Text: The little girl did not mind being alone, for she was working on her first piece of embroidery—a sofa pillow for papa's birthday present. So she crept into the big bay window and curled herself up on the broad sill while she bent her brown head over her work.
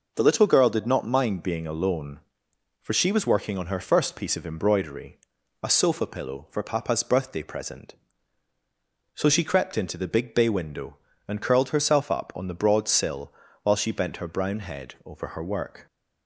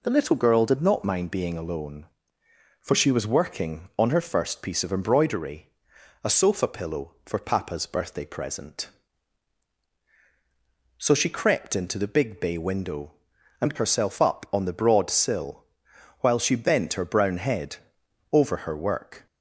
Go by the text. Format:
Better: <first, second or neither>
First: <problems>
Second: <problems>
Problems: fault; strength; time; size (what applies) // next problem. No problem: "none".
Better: first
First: pauses between "sill" and "while"; slight; at 13.3 s; 0.30 s long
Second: skips "curled"; at 13.7 s // pauses between "sill" and "while"; noticeable; at 15.6 s; 0.56 s long // pauses between "head" and "over"; noticeable; at 17.7 s; 0.56 s long